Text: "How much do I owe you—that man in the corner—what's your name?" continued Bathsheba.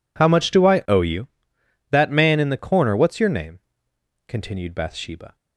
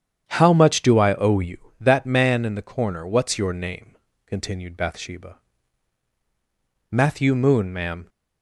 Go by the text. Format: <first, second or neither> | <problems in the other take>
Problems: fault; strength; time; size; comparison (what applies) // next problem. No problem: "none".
first | starts louder than the rest; strong; until 1.2 s; 9 dB // goes on to say "Matthew Moon ma'am"; noticeable; from 6.9 s on; 1.1 s long